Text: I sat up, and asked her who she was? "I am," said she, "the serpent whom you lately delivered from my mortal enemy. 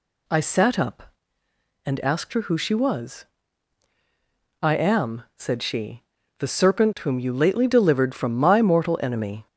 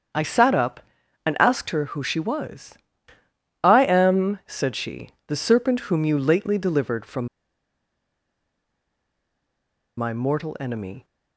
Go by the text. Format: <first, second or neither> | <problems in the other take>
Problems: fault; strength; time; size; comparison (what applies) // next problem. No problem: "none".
first | starts louder than the rest; strong; until 1.5 s; 7.5 dB // pauses between "from" and "my"; strong; at 7.2 s; 2.7 s long